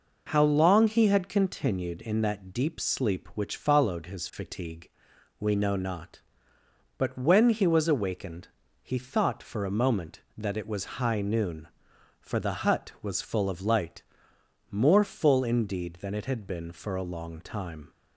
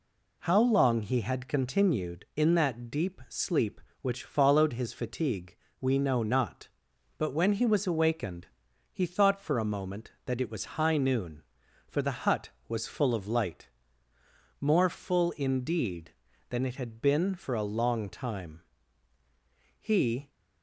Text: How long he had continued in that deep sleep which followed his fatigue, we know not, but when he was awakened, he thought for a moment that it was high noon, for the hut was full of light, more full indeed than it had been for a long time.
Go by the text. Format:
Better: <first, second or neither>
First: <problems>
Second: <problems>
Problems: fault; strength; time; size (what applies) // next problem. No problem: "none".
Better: first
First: none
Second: goes on to say "He"; from 19.7 s on; 0.52 s long